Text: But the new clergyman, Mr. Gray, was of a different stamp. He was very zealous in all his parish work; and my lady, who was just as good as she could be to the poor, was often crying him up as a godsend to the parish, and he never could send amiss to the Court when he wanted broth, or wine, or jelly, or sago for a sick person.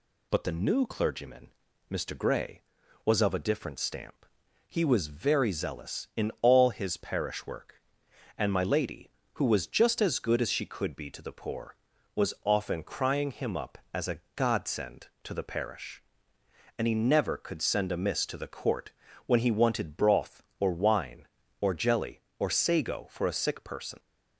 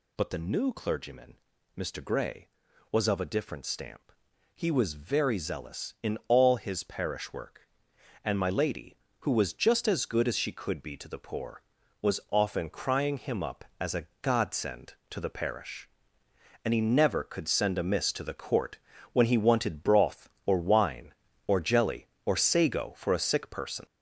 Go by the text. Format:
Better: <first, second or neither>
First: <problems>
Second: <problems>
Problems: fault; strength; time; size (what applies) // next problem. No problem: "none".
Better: first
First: pauses between "Court" and "when"; slight; at 18.9 s; 0.34 s long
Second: gets louder; noticeable; throughout; 5 dB // pauses between "Court" and "when"; slight; at 18.7 s; 0.34 s long